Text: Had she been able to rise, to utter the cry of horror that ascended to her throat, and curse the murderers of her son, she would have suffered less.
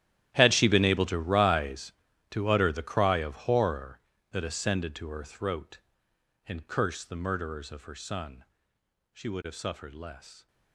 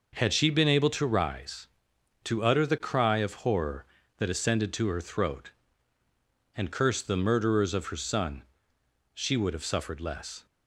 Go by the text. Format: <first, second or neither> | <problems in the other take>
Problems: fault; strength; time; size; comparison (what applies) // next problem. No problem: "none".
second | gets quieter; strong; throughout; 19.5 dB